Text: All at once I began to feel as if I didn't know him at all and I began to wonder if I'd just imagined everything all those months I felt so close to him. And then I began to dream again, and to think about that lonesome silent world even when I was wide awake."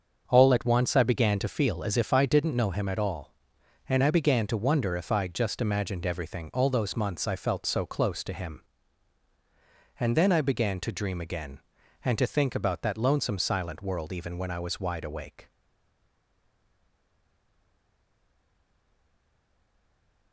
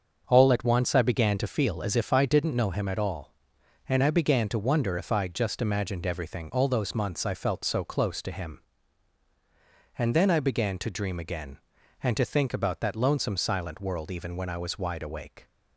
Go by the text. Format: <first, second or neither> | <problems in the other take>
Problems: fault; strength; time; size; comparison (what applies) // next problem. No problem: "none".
second | starts louder than the rest; until 1.3 s; 6.5 dB; also in the second // stays silent after the last word; strong; from 15.4 s on; 4.9 s long